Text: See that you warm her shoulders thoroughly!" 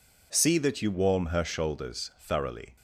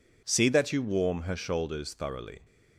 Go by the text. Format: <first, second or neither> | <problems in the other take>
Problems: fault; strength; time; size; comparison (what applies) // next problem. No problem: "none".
neither | none